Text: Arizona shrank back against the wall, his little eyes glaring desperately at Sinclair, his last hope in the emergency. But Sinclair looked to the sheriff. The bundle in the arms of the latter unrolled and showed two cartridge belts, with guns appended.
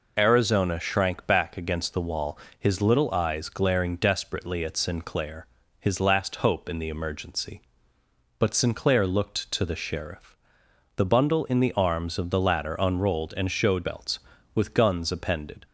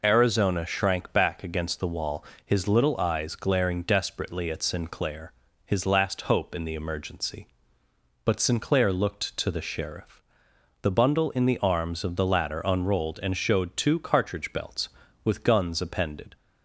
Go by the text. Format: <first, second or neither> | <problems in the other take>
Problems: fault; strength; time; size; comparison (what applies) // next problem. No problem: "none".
second | skips "two cartridge"; at 13.8 s